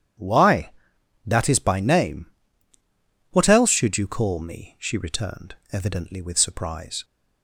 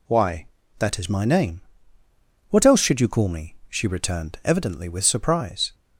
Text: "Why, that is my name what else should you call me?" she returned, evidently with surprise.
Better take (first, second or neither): second